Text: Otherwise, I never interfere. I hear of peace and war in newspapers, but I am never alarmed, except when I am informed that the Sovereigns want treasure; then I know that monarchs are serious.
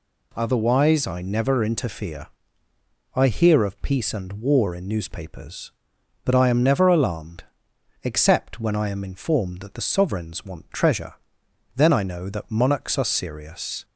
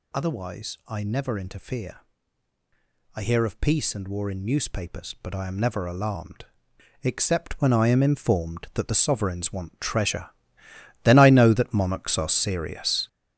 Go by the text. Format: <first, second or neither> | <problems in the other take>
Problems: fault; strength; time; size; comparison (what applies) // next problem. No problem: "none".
first | gets louder; strong; throughout; 8 dB